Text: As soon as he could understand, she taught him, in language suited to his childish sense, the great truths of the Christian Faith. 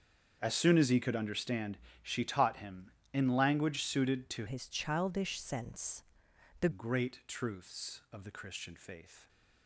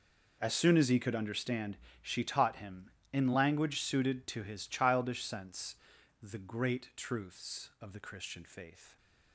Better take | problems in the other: second | starts louder than the rest; strong; until 1.4 s; 7 dB // changes voice from "his" to "the"; from 4.4 to 6.6 s; 2.2 s long

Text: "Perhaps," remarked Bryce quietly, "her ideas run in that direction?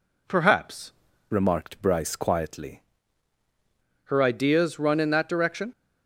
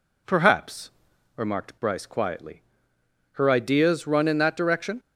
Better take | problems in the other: second | changes voice from "remarked" to "quietly"; from 1.3 to 2.8 s; 1.5 s long

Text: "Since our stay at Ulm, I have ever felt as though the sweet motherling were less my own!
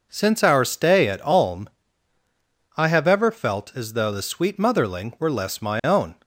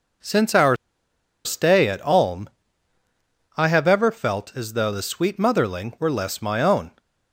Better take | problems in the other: first | pauses between "our" and "stay"; noticeable; at 0.7 s; 0.68 s long

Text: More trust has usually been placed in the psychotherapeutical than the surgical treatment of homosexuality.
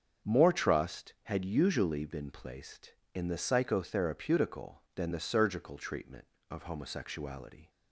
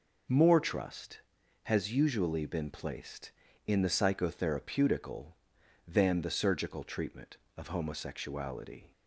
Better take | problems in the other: second | starts louder than the rest; until 1.3 s; 7 dB // says "had" for "has"; at 1.2 s

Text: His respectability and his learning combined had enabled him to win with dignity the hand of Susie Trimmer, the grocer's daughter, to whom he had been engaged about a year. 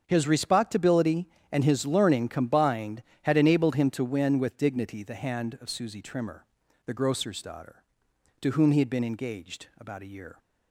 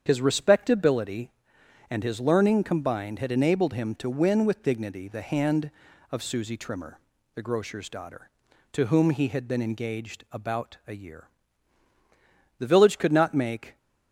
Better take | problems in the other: first | starts louder than the rest; strong; until 1.0 s; 8 dB; strong in the first // goes on to say "The village could not make"; noticeable; from 12.5 s on; 1.1 s long

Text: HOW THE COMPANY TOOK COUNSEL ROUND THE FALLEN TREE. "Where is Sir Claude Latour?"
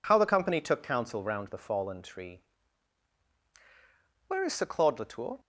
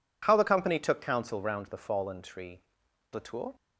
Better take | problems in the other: first | skips "Where is Sir Claude"; at 2.8 s

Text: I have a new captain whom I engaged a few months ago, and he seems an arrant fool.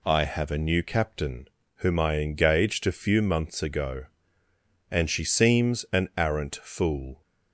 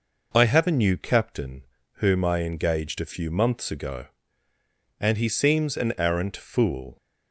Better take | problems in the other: second | pauses between "captain" and "whom"; slight; at 1.4 s; 0.30 s long; slight in the second // says "she" for "he"; at 5.0 s

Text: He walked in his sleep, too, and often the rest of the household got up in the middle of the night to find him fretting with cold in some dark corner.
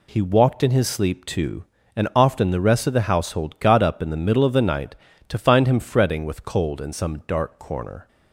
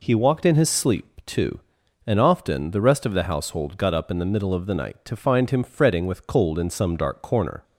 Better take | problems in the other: neither | none

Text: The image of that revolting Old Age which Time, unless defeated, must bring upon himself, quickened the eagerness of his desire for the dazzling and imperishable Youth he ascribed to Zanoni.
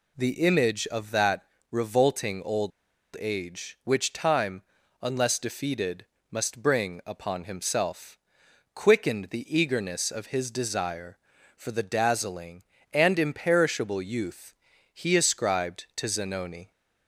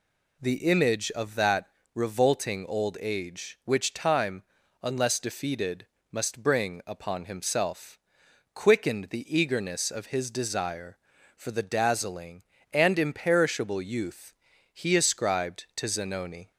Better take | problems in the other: second | pauses between "that" and "revolting"; slight; at 1.4 s; 0.30 s long; slight in the second // pauses between "Old" and "Age"; noticeable; at 2.7 s; 0.48 s long // pauses between "Youth" and "he"; at 14.5 s; 0.40 s long; also in the second

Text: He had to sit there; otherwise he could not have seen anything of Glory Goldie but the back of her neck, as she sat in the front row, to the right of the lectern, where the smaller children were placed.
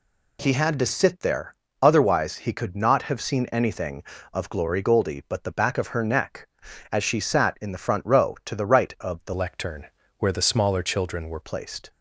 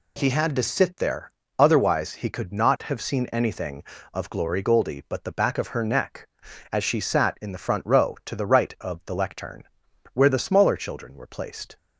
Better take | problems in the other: second | changes voice from "lectern" to "were"; from 9.3 to 11.4 s; 2.1 s long

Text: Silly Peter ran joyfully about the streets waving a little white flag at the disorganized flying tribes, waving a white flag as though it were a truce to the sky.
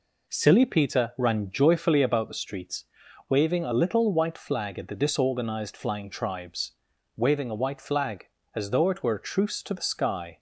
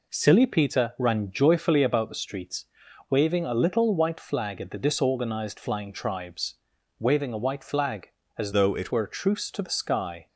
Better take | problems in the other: first | pauses between "streets" and "waving"; noticeable; at 2.6 s; 0.46 s long; noticeable in the first // changes voice from "though" to "it"; from 8.5 to 8.9 s; 0.4 s long

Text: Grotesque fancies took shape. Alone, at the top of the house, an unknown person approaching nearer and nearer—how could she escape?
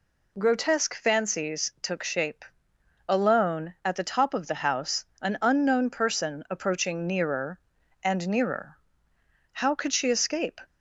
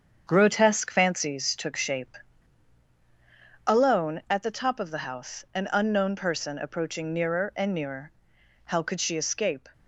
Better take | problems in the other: first | gets quieter; throughout; 6.5 dB

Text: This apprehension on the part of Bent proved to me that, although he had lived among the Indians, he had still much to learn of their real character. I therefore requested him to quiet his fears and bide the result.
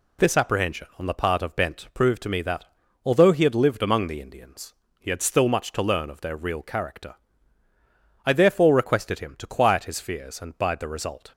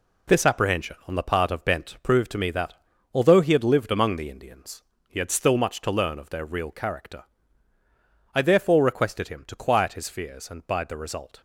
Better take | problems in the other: first | gets quieter; strong; throughout; 7.5 dB

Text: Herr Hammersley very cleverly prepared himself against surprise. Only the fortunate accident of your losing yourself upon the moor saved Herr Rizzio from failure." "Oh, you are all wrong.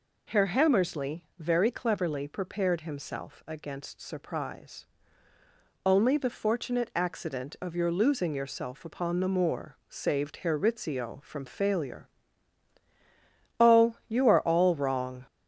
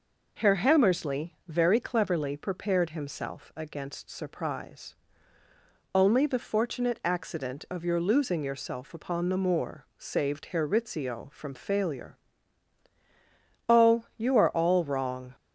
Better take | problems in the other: second | gets louder; throughout; 3.5 dB

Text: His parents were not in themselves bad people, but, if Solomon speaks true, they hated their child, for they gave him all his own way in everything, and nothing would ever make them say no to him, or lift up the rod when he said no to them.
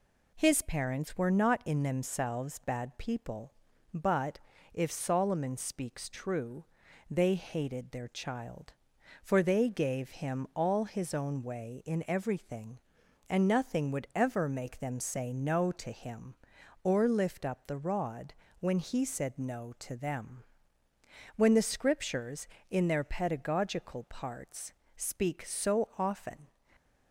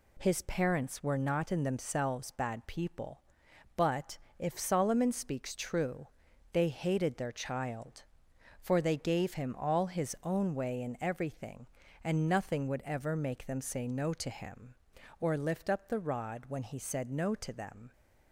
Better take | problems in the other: second | pauses between "rod" and "when"; slight; at 18.3 s; 0.26 s long // goes on to say "When the Scriptures in their pedagogical parts speak so often"; strong; from 21.3 s on; 5.1 s long

